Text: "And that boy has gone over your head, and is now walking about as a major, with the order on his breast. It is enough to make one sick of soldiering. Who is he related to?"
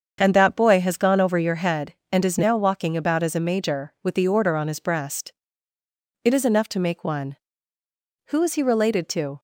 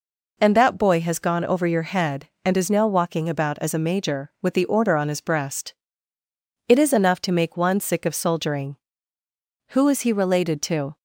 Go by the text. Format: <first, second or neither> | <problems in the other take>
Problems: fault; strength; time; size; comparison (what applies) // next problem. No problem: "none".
second | starts louder than the rest; until 1.2 s; 7 dB // skips "sick of soldiering"; at 7.8 s